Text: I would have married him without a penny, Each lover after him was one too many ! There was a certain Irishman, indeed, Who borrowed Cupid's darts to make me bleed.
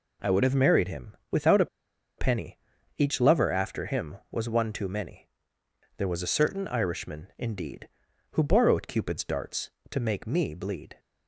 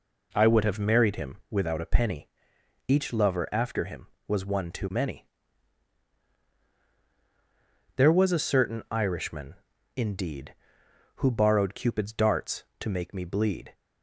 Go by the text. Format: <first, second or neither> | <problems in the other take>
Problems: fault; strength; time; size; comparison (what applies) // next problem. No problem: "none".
second | pauses between "him" and "without"; slight; at 1.1 s; 0.16 s long // pauses between "a" and "penny"; noticeable; at 1.6 s; 0.52 s long